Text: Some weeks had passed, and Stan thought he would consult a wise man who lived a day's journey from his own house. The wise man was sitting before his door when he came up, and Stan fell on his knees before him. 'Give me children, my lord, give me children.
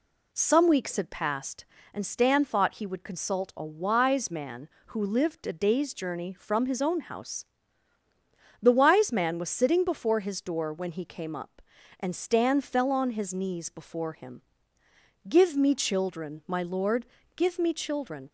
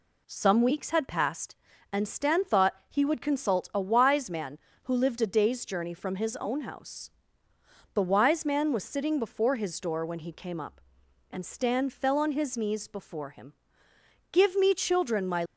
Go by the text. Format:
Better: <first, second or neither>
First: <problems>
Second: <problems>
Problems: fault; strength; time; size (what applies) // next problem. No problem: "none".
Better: first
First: none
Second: stops before "lord give me children"; at 15.4 s